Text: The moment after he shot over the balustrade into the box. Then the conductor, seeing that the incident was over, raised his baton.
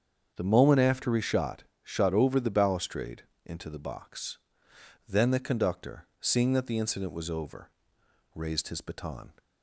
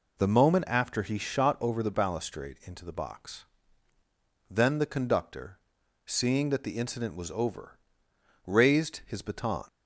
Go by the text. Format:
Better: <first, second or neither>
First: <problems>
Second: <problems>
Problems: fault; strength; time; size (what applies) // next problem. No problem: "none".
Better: second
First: starts louder than the rest; strong; until 1.3 s; 7 dB // says "shot" twice; at 1.8 s // pauses between "balustrade" and "into"; slight; at 3.2 s; 0.22 s long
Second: none